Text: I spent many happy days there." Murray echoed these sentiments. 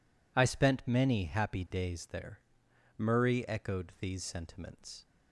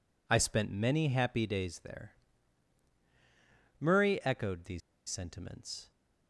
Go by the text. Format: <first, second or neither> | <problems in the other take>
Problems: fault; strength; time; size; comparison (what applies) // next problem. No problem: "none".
first | pauses between "these" and "sentiments"; slight; at 4.8 s; 0.28 s long